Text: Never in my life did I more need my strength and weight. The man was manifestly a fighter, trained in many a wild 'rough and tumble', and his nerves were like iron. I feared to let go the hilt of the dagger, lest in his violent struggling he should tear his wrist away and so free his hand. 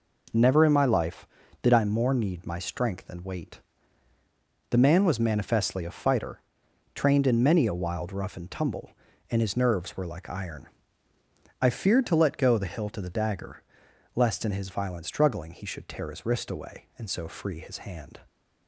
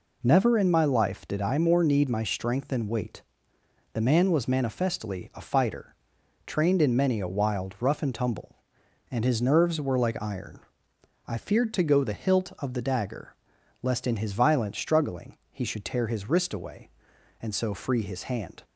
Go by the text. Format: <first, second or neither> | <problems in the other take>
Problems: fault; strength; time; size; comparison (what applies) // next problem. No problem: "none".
first | skips "let"; at 11.8 s